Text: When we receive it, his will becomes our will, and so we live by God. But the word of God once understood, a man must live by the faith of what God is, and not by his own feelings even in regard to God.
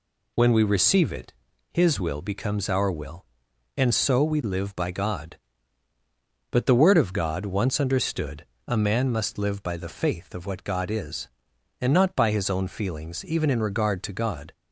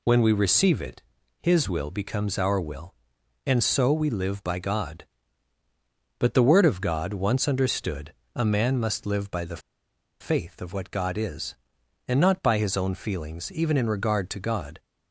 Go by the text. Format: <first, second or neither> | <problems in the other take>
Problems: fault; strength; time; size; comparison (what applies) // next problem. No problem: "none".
first | pauses between "the" and "faith"; noticeable; at 9.5 s; 0.62 s long